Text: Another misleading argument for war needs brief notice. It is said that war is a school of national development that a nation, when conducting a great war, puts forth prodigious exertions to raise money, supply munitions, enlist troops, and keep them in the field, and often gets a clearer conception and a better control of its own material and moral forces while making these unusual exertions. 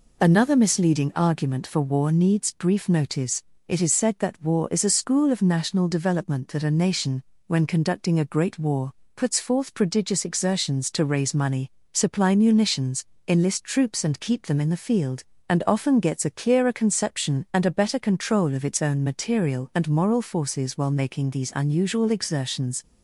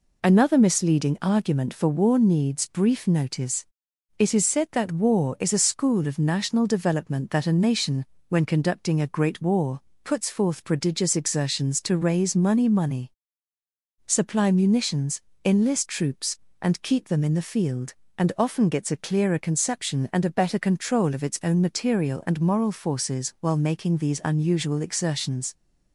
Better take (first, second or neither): first